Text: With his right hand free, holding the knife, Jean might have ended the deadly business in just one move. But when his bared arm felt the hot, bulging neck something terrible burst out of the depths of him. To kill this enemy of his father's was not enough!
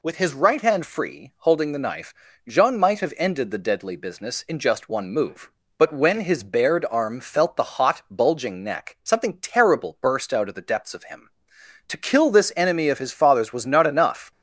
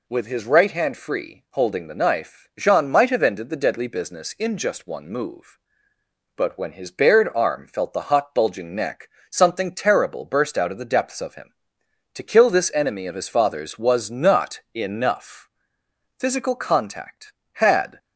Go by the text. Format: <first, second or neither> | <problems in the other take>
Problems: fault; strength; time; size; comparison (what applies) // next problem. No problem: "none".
first | pauses between "neck" and "something"; slight; at 9.0 s; 0.22 s long // goes on to say "Physical contact had"; strong; from 16.1 s on; 1.8 s long